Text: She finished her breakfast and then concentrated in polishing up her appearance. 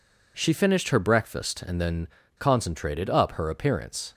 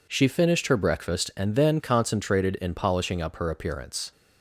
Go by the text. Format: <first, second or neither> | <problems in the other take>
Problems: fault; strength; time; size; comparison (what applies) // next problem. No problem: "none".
second | pauses between "then" and "concentrated"; slight; at 2.0 s; 0.30 s long // skips "in polishing"; at 3.0 s